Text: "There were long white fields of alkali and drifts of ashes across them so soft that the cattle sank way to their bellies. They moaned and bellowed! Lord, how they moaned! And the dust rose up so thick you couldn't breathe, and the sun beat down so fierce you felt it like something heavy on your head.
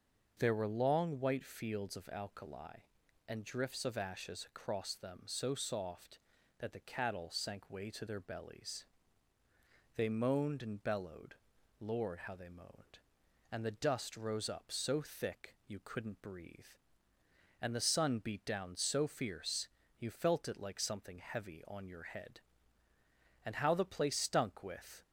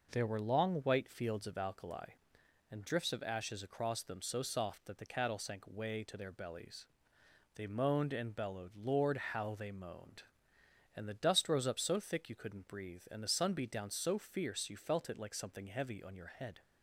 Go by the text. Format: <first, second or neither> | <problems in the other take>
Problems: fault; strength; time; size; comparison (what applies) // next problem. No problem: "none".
second | starts louder than the rest; until 1.3 s; 6.5 dB // pauses between "fierce" and "you"; slight; at 19.6 s; 0.30 s long // goes on to say "And how the place stunk with"; from 23.4 s on; 1.5 s long